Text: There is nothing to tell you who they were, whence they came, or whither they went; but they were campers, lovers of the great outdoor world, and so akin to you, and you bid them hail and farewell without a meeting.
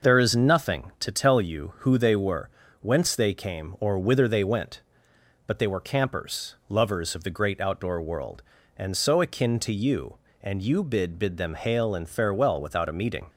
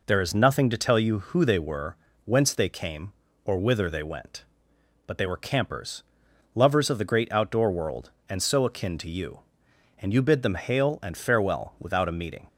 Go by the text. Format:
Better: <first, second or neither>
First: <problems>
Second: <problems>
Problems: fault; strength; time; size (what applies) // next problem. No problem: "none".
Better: second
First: says "bid" twice; at 11.1 s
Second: none